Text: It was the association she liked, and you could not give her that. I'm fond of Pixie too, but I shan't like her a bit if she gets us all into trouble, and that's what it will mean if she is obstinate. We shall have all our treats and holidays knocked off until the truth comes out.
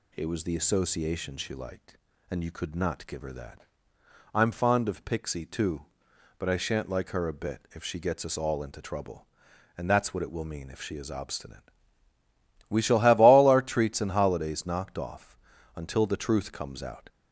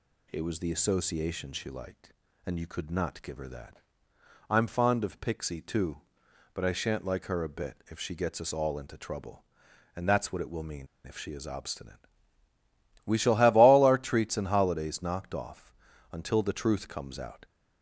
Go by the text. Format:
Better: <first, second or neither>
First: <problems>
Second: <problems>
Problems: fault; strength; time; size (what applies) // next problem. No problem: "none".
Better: first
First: pauses between "off" and "until"; at 15.3 s; 0.38 s long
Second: pauses between "mean" and "if"; slight; at 10.8 s; 0.20 s long // pauses between "off" and "until"; at 15.7 s; 0.38 s long